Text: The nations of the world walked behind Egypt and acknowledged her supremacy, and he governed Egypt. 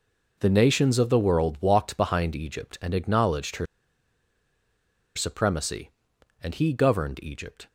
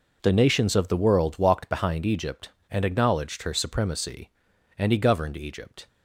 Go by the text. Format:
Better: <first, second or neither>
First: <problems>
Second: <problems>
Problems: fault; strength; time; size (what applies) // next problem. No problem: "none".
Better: second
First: pauses between "her" and "supremacy"; strong; at 3.6 s; 1.4 s long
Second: none